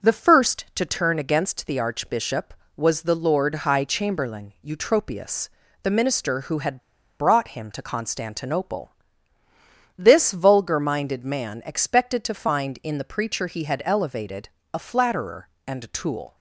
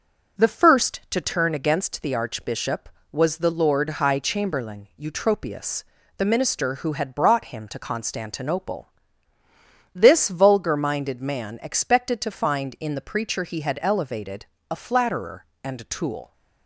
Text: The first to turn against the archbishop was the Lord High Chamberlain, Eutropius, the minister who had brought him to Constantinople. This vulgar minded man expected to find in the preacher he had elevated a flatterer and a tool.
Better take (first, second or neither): second